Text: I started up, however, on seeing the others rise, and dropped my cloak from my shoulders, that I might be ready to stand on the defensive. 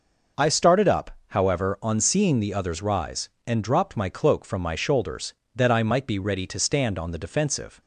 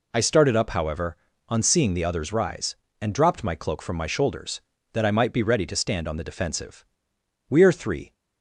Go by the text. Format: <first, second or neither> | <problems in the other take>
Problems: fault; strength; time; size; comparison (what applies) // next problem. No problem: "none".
first | goes on to say "We are three"; noticeable; from 7.4 s on; 0.64 s long